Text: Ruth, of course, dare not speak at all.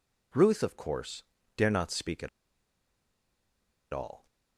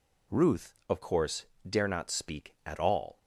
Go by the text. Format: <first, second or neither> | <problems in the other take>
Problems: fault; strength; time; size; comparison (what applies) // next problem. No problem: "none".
second | pauses between "at" and "all"; strong; at 2.2 s; 1.6 s long